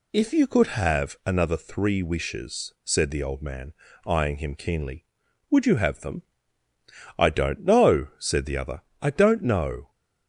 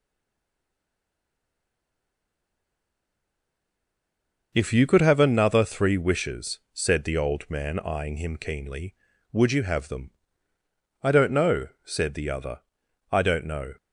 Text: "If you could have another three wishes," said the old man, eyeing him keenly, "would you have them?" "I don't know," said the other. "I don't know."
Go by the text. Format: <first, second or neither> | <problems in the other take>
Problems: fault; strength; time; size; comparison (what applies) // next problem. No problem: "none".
first | stays silent before the first word; strong; until 4.5 s; 4.5 s long